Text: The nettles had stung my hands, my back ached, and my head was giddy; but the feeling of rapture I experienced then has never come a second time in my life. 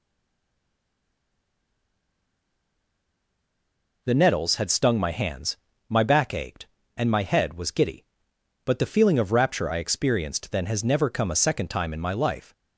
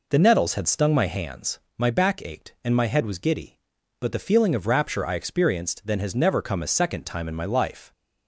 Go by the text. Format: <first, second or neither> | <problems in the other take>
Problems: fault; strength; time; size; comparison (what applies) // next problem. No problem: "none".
second | stays silent before the first word; strong; until 4.0 s; 4.0 s long